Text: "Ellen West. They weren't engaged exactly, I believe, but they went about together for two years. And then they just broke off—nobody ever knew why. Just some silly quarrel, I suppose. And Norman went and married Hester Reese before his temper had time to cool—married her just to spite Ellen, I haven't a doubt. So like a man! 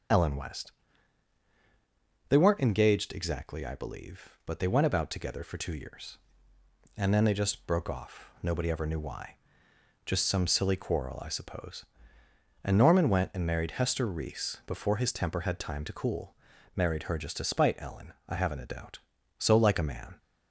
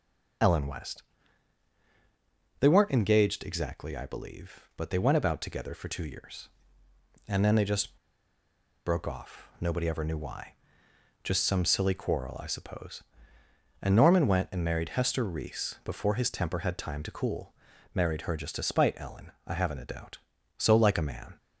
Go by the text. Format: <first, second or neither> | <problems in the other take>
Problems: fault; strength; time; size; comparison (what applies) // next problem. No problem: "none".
first | pauses between "just" and "broke"; noticeable; at 7.9 s; 0.88 s long